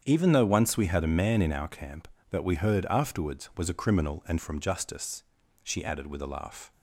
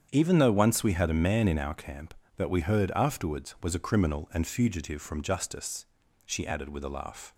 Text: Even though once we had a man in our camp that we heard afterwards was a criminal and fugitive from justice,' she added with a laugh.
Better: second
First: starts louder than the rest; strong; until 1.0 s; 8 dB // skips "fugitive"; at 4.3 s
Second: starts louder than the rest; strong; until 1.1 s; 8 dB

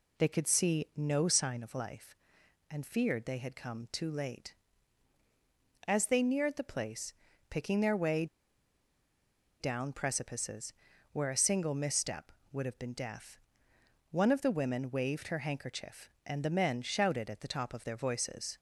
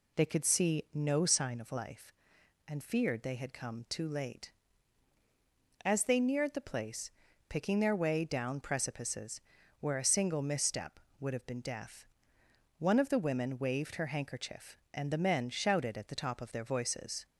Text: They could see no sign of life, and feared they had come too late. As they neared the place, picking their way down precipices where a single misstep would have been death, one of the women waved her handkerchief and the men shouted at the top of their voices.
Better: second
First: pauses between "way" and "down"; strong; at 8.2 s; 1.3 s long // pauses between "precipices" and "where"; at 10.7 s; 0.38 s long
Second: pauses between "precipices" and "where"; at 9.4 s; 0.38 s long

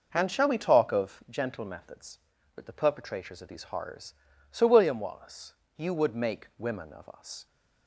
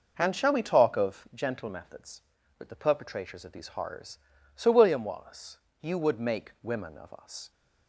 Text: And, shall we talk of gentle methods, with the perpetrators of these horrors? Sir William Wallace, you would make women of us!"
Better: neither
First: none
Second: none

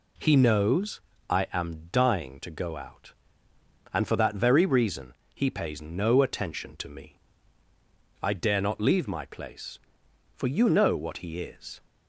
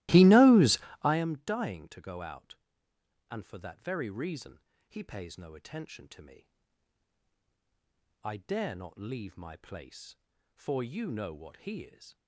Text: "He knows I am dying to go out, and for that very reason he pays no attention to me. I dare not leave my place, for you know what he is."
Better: first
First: pauses between "knows" and "I"; slight; at 1.0 s; 0.28 s long // pauses between "reason" and "he"; slight; at 5.1 s; 0.22 s long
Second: starts louder than the rest; strong; until 1.3 s; 17.5 dB // pauses between "knows" and "I"; slight; at 0.7 s; 0.24 s long // pauses between "reason" and "he"; slight; at 4.5 s; 0.30 s long

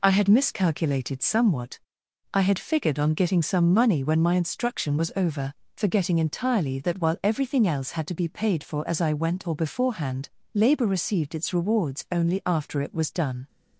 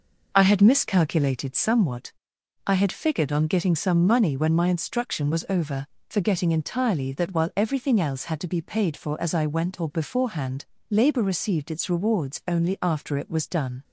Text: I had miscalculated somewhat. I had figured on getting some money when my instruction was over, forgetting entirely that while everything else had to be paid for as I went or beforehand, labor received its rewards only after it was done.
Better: first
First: none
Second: starts louder than the rest; noticeable; until 1.4 s; 5.5 dB

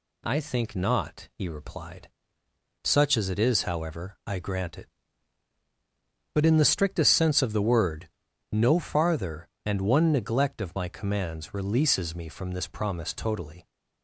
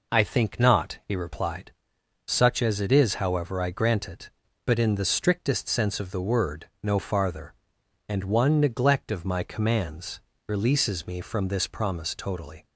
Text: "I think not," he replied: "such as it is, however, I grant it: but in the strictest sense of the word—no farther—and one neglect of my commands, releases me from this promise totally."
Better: neither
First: none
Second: none

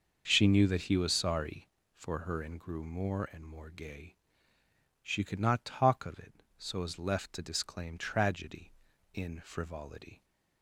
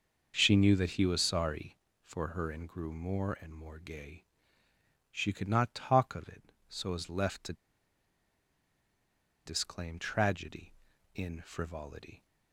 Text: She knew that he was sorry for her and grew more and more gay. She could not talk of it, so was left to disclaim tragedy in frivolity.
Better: first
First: starts louder than the rest; noticeable; until 1.2 s; 6 dB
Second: starts louder than the rest; noticeable; until 1.3 s; 6 dB // pauses between "to" and "disclaim"; strong; at 7.5 s; 1.9 s long

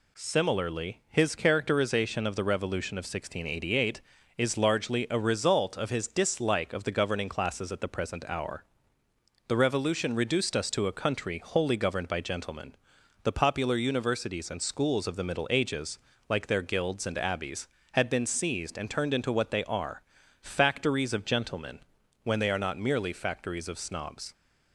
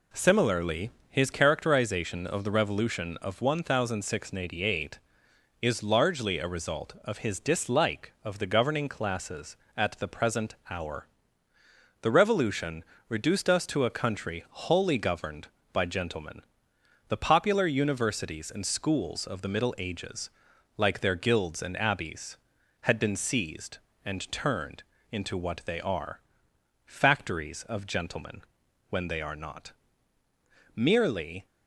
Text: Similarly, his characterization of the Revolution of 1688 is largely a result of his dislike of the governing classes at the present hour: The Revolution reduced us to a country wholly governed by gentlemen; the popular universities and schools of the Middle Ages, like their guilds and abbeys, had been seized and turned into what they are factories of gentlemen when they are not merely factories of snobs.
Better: first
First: pauses between "are" and "factories"; at 20.0 s; 0.38 s long // pauses between "gentlemen" and "when"; at 21.7 s; 0.44 s long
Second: pauses between "Revolution" and "reduced"; slight; at 12.8 s; 0.24 s long // pauses between "turned" and "into"; slight; at 24.8 s; 0.26 s long // pauses between "are" and "factories"; noticeable; at 26.1 s; 0.66 s long // pauses between "gentlemen" and "when"; noticeable; at 28.4 s; 0.48 s long // pauses between "not" and "merely"; at 29.7 s; 1.0 s long // stops before "factories of snobs"; at 31.4 s

